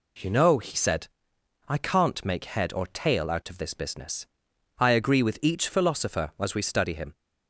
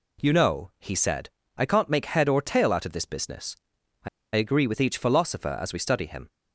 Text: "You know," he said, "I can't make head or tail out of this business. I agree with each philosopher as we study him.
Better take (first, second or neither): first